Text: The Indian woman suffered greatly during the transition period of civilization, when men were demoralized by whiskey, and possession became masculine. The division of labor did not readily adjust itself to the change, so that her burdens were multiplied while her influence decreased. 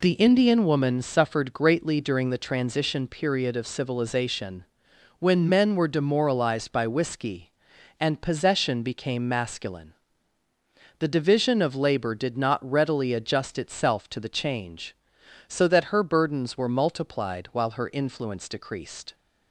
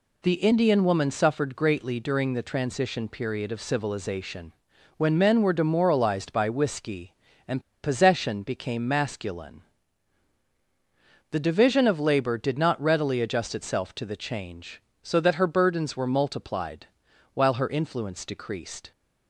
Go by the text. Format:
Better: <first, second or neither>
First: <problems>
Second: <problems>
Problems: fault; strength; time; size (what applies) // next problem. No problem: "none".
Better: first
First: none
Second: pauses between "and" and "possession"; slight; at 7.6 s; 0.21 s long // pauses between "multiplied" and "while"; noticeable; at 16.8 s; 0.46 s long